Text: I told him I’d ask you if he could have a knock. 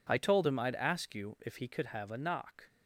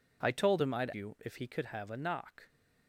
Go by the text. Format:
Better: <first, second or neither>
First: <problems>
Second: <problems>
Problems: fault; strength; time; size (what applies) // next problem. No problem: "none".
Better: first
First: none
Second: skips "ask"; at 0.9 s